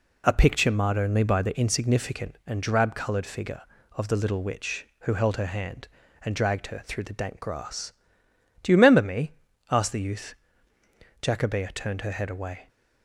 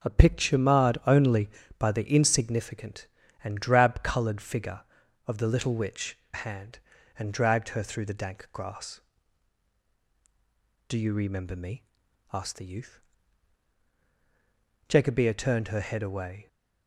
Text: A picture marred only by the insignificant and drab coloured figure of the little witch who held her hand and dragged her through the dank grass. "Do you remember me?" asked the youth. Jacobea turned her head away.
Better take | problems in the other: first | starts louder than the rest; until 1.1 s; 7 dB // skips "who held her"; at 6.2 s

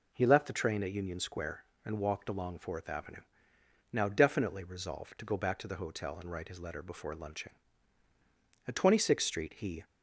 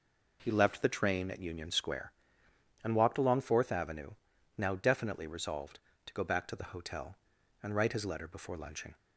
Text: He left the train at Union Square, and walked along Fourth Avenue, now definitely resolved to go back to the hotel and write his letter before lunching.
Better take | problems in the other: second | goes on to say "At Twenty sixth Street he"; noticeable; from 8.6 s on; 1.1 s long

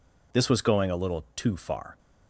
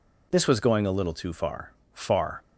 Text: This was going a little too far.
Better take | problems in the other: first | says "far" twice; at 1.9 s

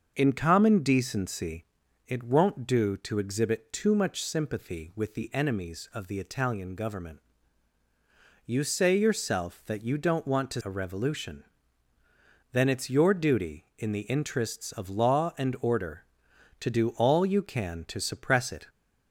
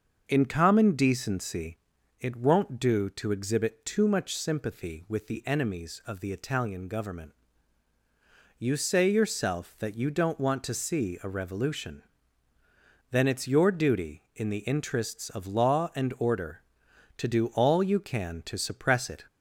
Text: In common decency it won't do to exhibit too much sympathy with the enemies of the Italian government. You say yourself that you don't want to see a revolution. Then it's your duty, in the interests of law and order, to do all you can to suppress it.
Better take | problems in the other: second | starts louder than the rest; until 1.1 s; 6.5 dB; also in the second // pauses between "decency" and "it"; at 1.6 s; 0.42 s long; also in the second // skips "see"; at 10.6 s

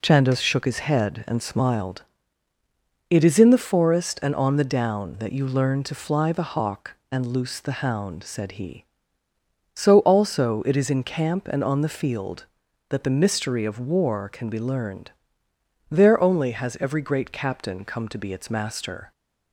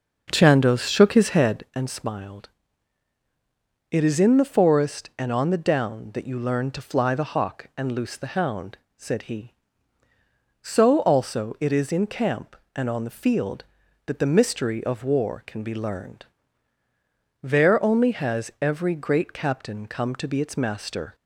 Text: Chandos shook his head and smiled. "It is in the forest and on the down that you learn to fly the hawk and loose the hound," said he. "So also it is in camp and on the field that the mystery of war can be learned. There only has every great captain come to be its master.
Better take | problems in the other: first | starts louder than the rest; until 1.7 s; 6 dB

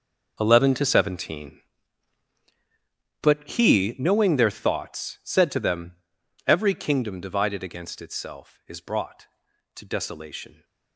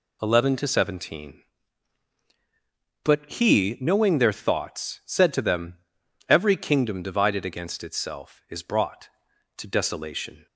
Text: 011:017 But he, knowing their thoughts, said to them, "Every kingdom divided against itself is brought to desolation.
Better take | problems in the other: second | gets quieter; strong; throughout; 14.5 dB

